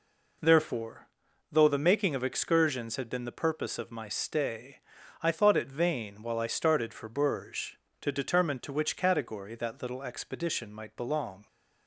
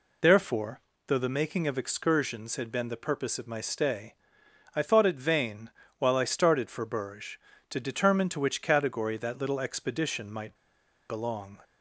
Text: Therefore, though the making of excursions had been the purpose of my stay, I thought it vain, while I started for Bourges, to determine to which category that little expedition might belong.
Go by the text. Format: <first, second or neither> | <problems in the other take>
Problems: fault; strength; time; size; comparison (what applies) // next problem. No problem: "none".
first | pauses between "might" and "belong"; noticeable; at 10.5 s; 0.55 s long